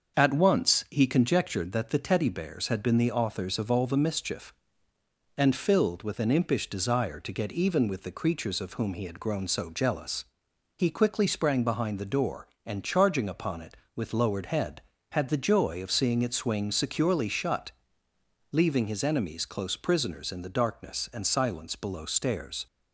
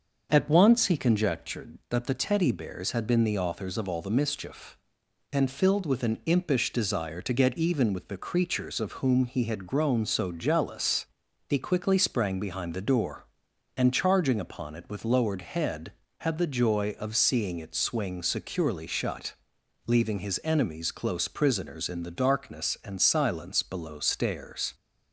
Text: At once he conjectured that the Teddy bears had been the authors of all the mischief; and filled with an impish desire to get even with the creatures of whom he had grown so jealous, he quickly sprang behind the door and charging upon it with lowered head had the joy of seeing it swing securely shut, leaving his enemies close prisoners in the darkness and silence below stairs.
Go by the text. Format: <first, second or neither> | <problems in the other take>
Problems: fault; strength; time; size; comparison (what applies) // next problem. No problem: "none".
neither | starts louder than the rest; the same in both